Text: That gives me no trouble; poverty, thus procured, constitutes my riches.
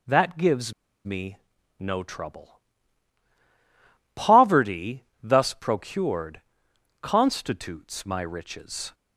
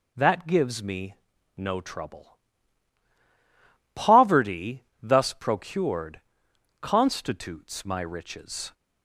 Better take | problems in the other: second | pauses between "gives" and "me"; slight; at 0.7 s; 0.32 s long // pauses between "me" and "no"; at 1.3 s; 0.42 s long; also in the second

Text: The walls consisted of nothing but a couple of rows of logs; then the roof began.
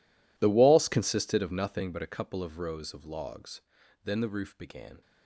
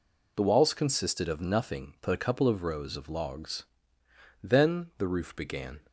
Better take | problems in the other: second | gets quieter; strong; throughout; 20 dB

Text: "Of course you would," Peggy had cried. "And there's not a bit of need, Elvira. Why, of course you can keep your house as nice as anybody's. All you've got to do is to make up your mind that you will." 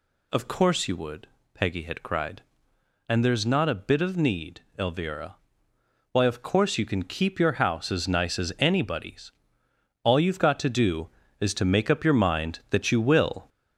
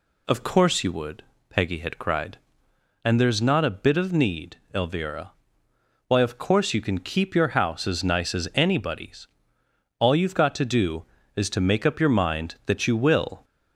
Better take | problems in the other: second | gets louder; noticeable; throughout; 4.5 dB

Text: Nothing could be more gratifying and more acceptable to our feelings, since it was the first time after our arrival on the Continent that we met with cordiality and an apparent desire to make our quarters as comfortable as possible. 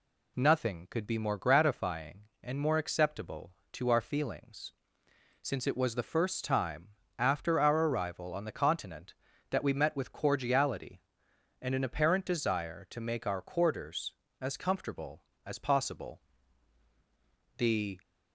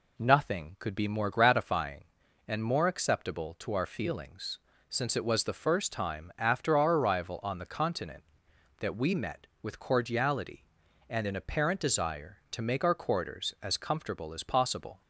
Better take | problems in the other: second | pauses between "time" and "after"; slight; at 6.8 s; 0.30 s long // goes on to say "The"; slight; from 17.5 s on; 0.40 s long

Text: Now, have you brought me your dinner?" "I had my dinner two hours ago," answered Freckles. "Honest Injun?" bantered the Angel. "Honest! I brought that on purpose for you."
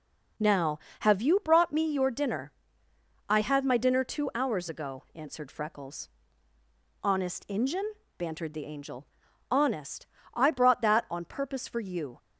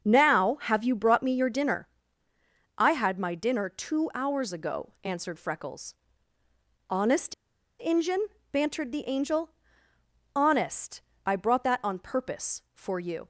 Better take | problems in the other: first | starts louder than the rest; until 1.0 s; 6.5 dB // pauses between "Honest" and "Injun"; noticeable; at 7.3 s; 0.47 s long

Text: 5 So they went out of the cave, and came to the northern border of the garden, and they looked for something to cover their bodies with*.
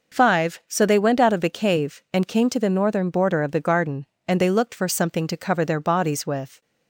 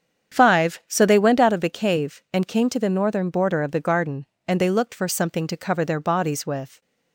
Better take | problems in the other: first | starts louder than the rest; strong; until 1.5 s; 8 dB

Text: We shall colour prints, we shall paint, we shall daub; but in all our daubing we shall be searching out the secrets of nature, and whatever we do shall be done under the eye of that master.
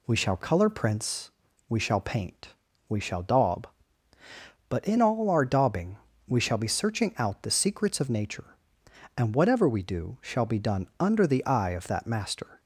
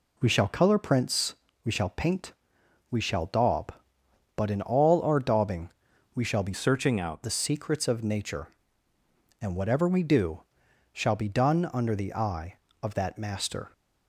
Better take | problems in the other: first | pauses between "daubing" and "we"; noticeable; at 5.6 s; 0.46 s long; slight in the first // changes voice from "searching" to "out"; from 6.5 to 7.2 s; 0.7 s long // pauses between "do" and "shall"; noticeable; at 10.4 s; 0.50 s long

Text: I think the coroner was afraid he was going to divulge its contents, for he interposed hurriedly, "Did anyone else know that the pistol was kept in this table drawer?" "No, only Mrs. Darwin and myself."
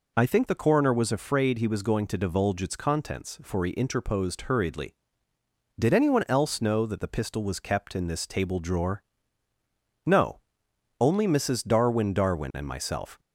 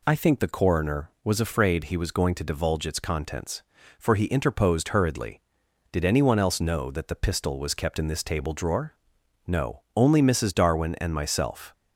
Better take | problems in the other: second | says "Darwin" twice; at 12.1 s

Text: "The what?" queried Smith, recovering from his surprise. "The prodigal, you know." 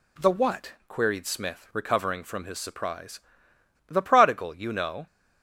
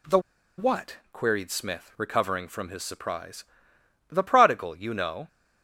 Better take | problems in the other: first | pauses between "The" and "what"; at 0.1 s; 0.38 s long

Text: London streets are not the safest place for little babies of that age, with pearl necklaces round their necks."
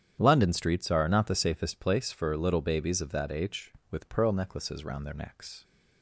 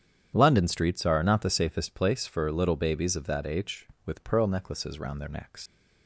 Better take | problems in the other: first | starts louder than the rest; strong; until 1.3 s; 9 dB; strong in the first // leaves "necks" unfinished; at 5.6 s; 120 ms

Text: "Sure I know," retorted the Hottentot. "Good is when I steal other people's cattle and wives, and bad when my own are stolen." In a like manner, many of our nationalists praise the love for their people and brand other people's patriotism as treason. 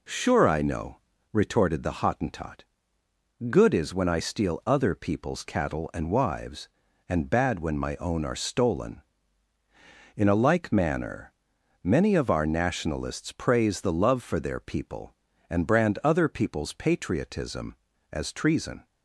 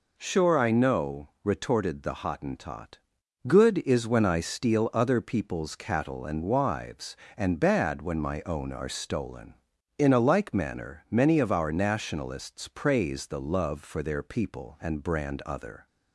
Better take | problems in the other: first | stops before "people's patriotism as treason"; at 15.8 s

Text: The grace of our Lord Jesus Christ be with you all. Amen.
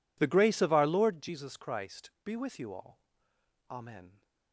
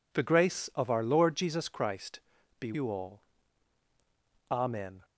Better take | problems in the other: first | pauses between "Christ" and "be"; at 2.1 s; 0.40 s long // skips "with"; at 2.7 s

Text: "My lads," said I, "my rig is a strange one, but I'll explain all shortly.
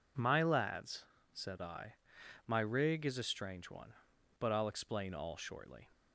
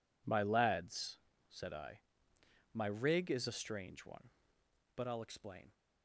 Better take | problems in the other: first | stops before "all shortly"; at 5.7 s

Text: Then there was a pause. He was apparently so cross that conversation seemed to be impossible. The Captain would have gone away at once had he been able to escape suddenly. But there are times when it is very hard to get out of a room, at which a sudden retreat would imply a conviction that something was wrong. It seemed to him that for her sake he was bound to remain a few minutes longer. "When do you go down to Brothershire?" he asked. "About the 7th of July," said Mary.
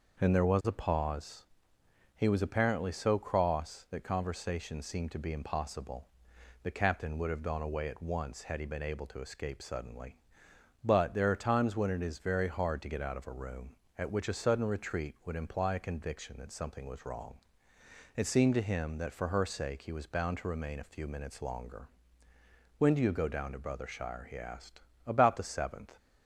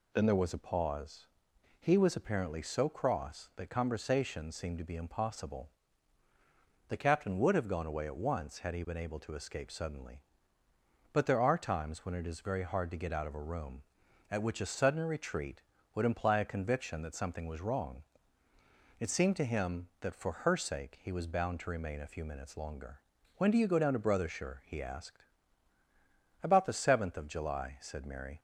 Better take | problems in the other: second | stops before "of July said Mary"; at 25.9 s

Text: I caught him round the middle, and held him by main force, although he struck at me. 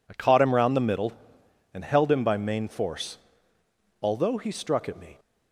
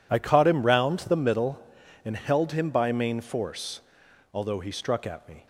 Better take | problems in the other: neither | none

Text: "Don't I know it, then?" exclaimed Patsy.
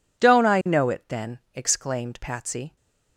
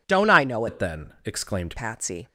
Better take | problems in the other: first | changes voice from "it" to "exclaimed"; from 0.6 to 1.7 s; 1.1 s long

